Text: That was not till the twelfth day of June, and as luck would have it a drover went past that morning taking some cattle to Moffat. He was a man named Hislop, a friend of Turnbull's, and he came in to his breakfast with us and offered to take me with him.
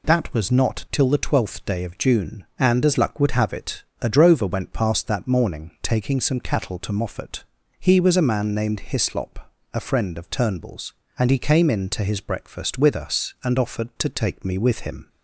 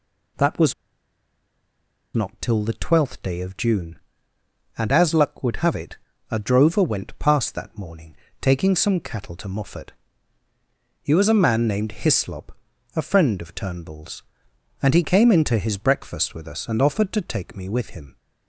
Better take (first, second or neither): first